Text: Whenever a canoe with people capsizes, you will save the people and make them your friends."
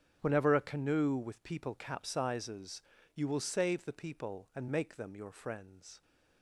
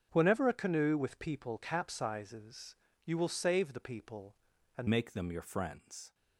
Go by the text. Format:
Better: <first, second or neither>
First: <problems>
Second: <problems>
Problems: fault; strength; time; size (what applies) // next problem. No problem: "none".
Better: first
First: starts louder than the rest; strong; until 1.2 s; 7.5 dB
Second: starts louder than the rest; until 1.1 s; 7 dB // changes voice at "make"; from 4.8 s on; 1.3 s long